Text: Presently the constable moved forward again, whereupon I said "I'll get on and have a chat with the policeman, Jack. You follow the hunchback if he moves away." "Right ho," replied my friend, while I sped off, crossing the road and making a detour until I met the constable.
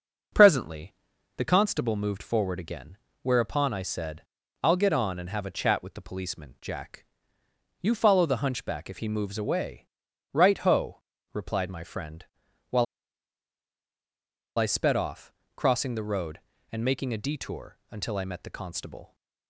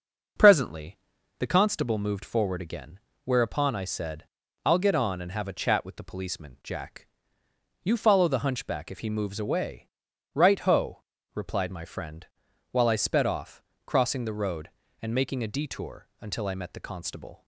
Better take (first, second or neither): second